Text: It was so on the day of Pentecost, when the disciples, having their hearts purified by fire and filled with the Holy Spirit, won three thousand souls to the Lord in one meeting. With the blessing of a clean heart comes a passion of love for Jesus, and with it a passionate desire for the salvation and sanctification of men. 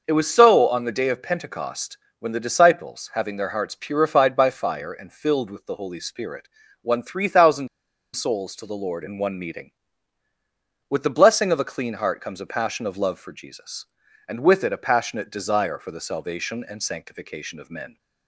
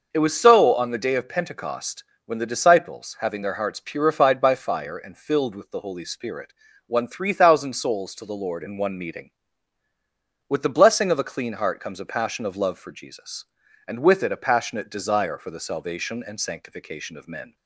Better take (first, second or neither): second